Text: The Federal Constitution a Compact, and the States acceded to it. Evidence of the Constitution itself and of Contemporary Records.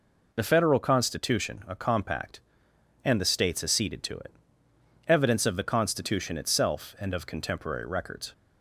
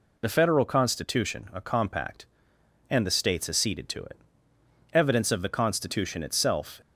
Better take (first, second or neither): first